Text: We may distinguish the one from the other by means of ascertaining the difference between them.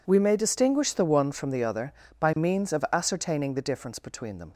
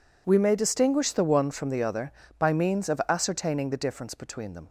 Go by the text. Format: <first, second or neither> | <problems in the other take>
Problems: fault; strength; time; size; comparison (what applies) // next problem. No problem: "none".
neither | none